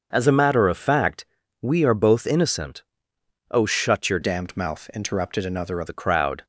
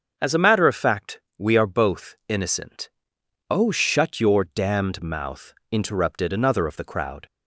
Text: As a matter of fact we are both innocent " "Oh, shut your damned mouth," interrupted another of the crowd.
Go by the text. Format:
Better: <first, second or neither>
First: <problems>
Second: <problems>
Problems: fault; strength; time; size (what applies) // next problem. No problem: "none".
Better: second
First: pauses between "fact" and "we"; at 1.2 s; 0.38 s long // changes voice from "damned" to "of"; from 4.2 to 5.8 s; 1.6 s long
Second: pauses between "fact" and "we"; slight; at 1.2 s; 0.16 s long